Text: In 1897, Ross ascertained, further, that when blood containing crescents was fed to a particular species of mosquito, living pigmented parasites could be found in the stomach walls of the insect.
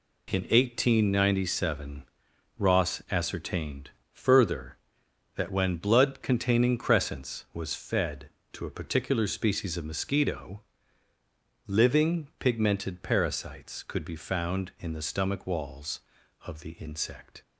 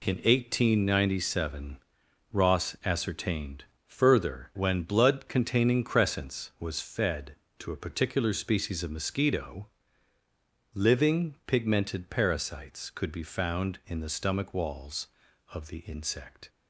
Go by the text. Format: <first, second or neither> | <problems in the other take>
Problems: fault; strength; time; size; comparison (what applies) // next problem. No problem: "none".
first | skips "that"; at 4.5 s